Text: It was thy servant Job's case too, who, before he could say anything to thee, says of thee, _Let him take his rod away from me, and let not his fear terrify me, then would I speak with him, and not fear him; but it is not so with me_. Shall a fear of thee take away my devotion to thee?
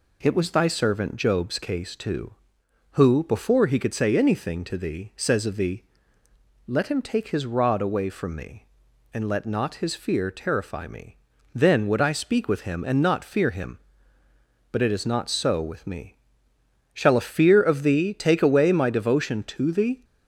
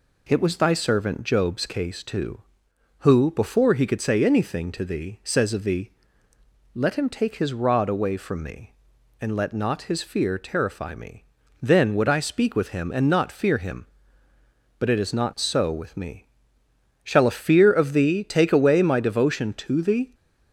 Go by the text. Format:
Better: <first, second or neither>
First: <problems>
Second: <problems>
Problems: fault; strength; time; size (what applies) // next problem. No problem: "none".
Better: neither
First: none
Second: none